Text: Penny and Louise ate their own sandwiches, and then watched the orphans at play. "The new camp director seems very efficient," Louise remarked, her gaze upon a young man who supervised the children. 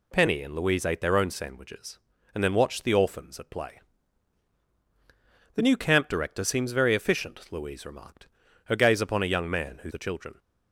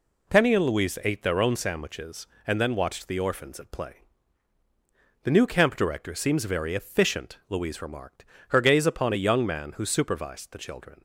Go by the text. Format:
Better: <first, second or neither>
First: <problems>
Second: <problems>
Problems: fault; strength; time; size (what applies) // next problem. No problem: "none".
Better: second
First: skips "supervised"; at 9.9 s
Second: none